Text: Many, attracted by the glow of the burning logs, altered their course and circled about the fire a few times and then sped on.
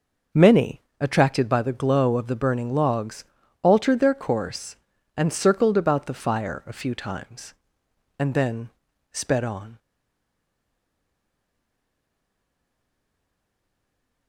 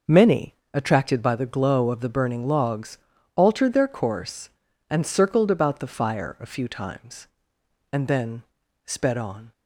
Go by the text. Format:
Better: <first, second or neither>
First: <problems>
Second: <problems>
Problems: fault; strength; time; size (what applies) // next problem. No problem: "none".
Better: second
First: pauses between "then" and "sped"; at 8.7 s; 0.42 s long // stays silent after the last word; strong; from 9.7 s on; 4.5 s long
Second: pauses between "then" and "sped"; at 8.4 s; 0.42 s long